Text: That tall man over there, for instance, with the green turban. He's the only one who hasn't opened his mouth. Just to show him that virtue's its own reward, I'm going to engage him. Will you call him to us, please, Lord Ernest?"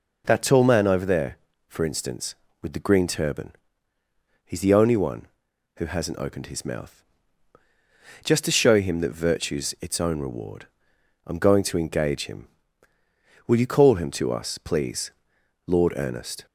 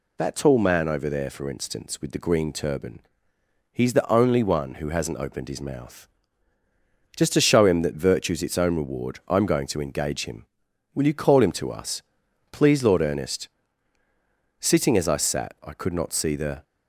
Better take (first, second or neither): first